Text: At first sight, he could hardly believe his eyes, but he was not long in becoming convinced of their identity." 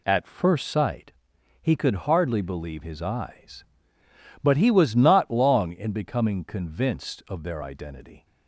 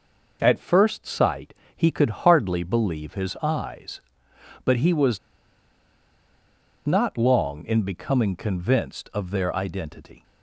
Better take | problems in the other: first | pauses between "was" and "not"; strong; at 5.1 s; 1.6 s long

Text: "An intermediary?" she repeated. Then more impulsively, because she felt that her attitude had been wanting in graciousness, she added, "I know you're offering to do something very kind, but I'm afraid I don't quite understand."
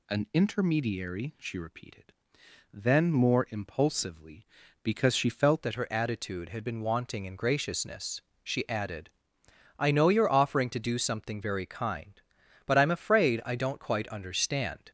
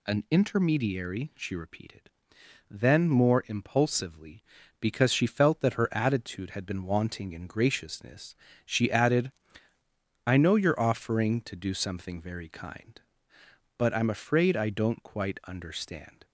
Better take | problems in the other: second | changes voice at "that"; from 5.6 s on; 9.3 s long

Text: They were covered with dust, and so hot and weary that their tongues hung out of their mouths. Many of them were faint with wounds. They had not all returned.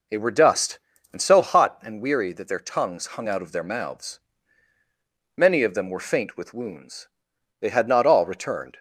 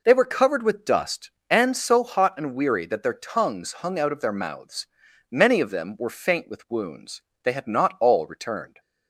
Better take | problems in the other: second | skips "covered with"; at 0.3 s

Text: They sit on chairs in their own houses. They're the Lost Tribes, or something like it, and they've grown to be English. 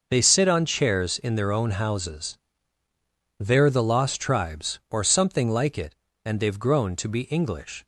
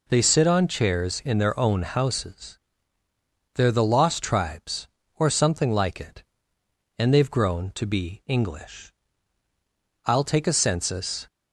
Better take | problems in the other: first | goes on to say "I'll take a census"; noticeable; from 10.0 s on; 1.2 s long

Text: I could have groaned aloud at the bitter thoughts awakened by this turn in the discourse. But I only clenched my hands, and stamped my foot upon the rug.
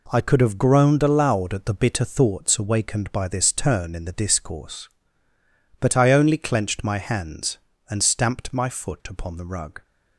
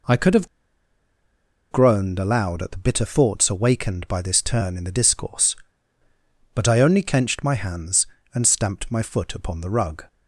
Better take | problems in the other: first | pauses between "have" and "groaned"; strong; at 0.4 s; 1.2 s long

